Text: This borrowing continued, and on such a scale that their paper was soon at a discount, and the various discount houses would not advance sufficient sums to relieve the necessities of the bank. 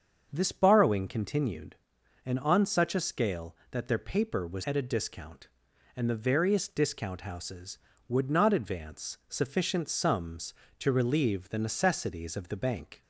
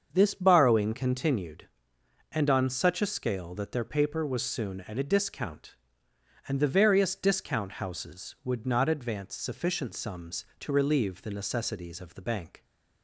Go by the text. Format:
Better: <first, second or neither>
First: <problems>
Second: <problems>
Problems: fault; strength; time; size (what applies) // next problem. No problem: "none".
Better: second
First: starts louder than the rest; until 1.3 s; 7 dB // skips "soon"; at 4.6 s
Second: starts louder than the rest; until 1.1 s; 7 dB